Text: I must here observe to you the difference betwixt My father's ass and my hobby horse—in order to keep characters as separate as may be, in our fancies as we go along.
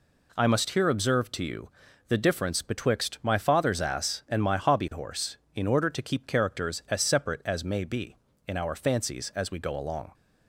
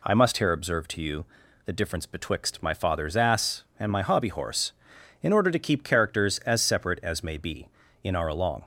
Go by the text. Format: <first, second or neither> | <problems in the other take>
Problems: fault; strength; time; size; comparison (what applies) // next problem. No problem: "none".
first | pauses between "you" and "the"; at 1.2 s; 0.40 s long; also in the first // skips "fancies as we go"; at 8.2 s